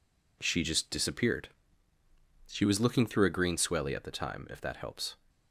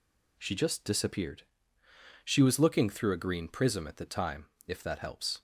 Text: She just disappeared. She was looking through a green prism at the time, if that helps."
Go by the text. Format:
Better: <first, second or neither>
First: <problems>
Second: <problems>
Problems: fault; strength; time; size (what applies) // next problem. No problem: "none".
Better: second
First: says "swelly" for "prism"; at 3.5 s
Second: none